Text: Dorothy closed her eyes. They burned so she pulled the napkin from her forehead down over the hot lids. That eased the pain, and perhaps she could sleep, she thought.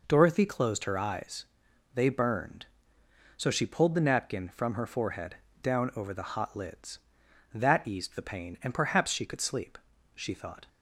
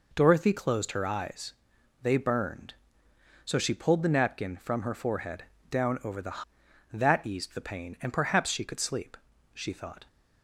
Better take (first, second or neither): first